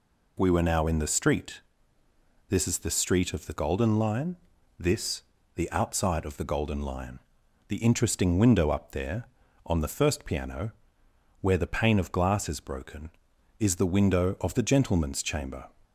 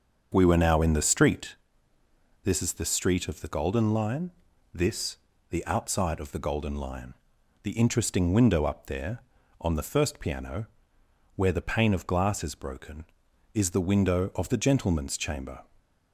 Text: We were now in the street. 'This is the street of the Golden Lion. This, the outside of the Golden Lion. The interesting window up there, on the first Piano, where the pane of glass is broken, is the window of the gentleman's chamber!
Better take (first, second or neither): first